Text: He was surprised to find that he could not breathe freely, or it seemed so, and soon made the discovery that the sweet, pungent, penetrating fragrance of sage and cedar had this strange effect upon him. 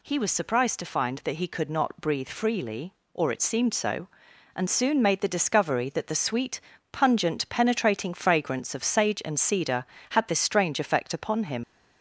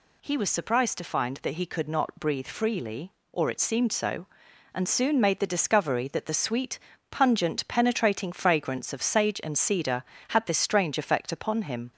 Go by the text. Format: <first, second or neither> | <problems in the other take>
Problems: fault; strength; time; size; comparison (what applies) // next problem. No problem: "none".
second | leaves "him" unfinished; at 11.6 s; 100 ms